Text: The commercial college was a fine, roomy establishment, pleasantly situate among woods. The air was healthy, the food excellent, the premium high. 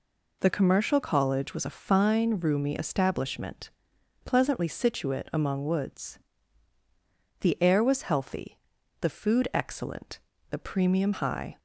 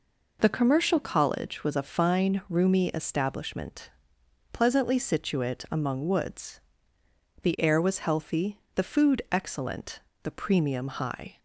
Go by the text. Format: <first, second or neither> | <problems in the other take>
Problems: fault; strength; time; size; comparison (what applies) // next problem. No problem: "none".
neither | none